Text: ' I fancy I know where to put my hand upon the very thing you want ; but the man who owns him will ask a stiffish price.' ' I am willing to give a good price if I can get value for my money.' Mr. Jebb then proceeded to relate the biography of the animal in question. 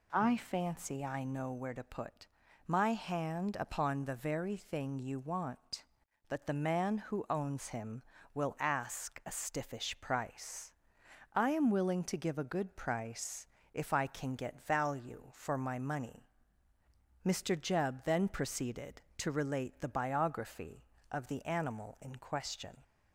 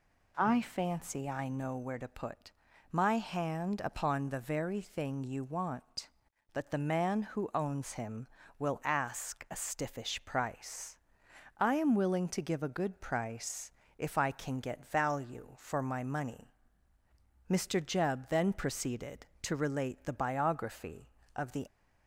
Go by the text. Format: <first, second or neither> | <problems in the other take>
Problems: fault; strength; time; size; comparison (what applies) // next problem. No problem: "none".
first | pauses between "put" and "my"; at 2.5 s; 0.40 s long; also in the first // pauses between "price" and "if"; slight; at 13.7 s; 0.26 s long; slight in the first // stops before "animal in question"; at 21.6 s